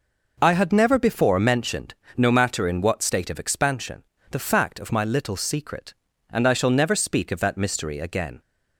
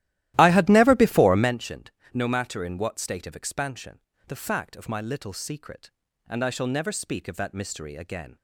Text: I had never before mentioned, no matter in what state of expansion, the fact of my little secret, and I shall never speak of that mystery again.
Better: first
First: none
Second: starts louder than the rest; strong; until 1.6 s; 14.5 dB

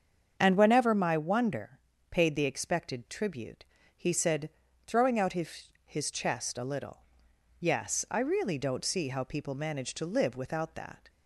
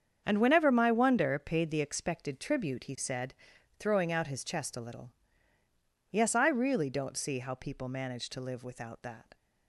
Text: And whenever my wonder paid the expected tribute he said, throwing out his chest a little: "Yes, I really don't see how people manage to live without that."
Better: second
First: starts louder than the rest; until 1.4 s; 7 dB // pauses between "wonder" and "paid"; slight; at 1.7 s; 0.30 s long // pauses between "tribute" and "he"; slight; at 3.6 s; 0.36 s long // says "his" twice; at 5.8 s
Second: starts louder than the rest; strong; until 1.2 s; 7.5 dB

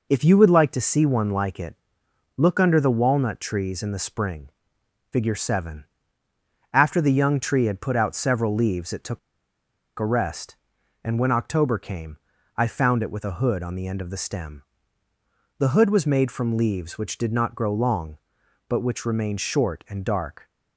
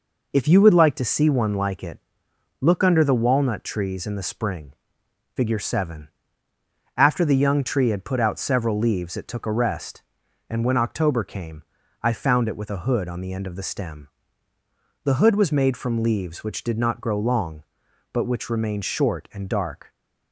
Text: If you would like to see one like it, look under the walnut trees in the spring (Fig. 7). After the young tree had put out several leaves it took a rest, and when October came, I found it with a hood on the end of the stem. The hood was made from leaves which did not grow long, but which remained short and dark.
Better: second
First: pauses between "took" and "a"; noticeable; at 9.1 s; 0.80 s long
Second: none

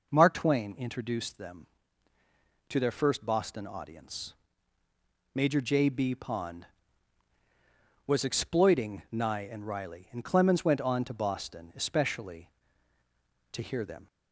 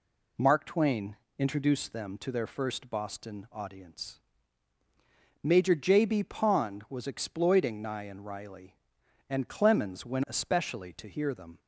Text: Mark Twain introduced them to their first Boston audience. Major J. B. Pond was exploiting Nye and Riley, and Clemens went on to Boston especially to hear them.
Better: first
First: none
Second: pauses between "Twain" and "introduced"; slight; at 1.1 s; 0.22 s long // skips "on to Boston"; at 10.2 s

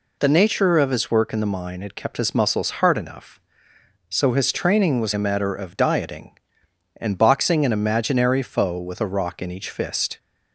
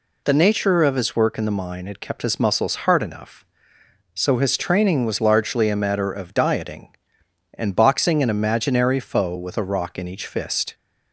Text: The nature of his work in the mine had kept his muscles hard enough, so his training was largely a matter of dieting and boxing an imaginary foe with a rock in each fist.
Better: second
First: skips "largely"; at 5.1 s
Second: none

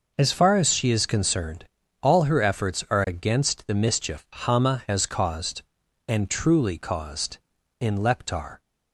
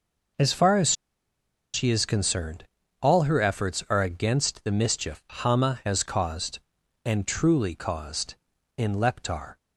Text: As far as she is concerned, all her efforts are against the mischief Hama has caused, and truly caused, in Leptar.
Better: first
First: none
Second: pauses between "as" and "she"; noticeable; at 0.9 s; 0.81 s long

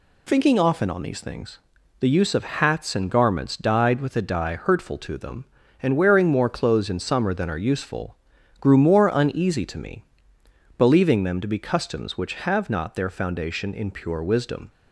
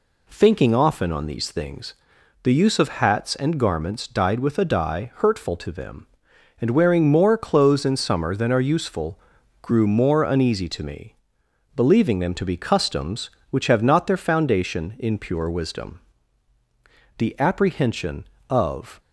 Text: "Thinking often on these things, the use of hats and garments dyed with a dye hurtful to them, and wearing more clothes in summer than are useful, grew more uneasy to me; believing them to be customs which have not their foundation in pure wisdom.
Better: first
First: none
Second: goes on to say "The apprehension of"; strong; from 17.1 s on; 1.8 s long

